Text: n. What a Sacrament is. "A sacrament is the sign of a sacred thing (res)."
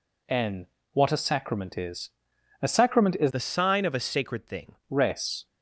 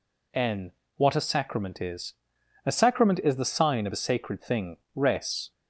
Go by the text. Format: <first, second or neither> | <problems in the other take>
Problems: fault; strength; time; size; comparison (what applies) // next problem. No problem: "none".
second | changes voice from "the" to "thing"; from 3.3 to 4.7 s; 1.4 s long